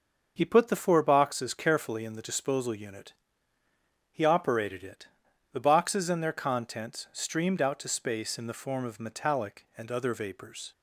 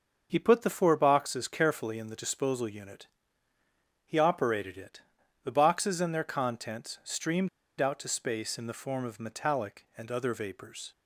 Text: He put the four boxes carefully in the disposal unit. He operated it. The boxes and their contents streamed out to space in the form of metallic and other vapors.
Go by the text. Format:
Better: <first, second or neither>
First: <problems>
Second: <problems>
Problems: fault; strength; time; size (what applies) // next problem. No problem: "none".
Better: first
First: starts louder than the rest; until 1.3 s; 6.5 dB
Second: starts louder than the rest; until 1.3 s; 6.5 dB // pauses between "streamed" and "out"; slight; at 7.4 s; 0.30 s long